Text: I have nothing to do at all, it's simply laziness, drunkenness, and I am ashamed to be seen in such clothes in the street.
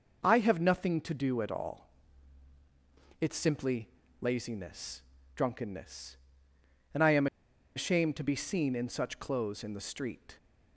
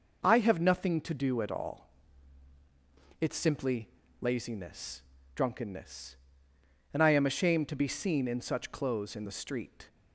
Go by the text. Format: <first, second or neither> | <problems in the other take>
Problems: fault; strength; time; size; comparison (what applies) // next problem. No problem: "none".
second | pauses between "simply" and "laziness"; slight; at 3.8 s; 0.32 s long; slight in the second // pauses between "am" and "ashamed"; noticeable; at 7.2 s; 0.49 s long